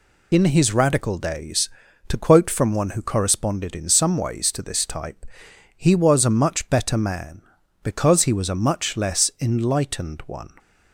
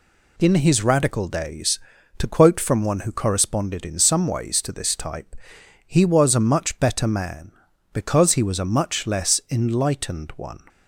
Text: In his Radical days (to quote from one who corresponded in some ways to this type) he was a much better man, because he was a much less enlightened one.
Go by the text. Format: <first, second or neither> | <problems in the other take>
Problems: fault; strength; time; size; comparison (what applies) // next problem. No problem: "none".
second | loses the start of "In"; at 0.3 s; 35 ms